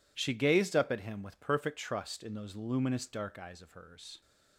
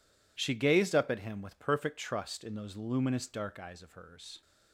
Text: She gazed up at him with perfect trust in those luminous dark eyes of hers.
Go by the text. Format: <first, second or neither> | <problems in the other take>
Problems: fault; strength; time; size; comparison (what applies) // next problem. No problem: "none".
neither | none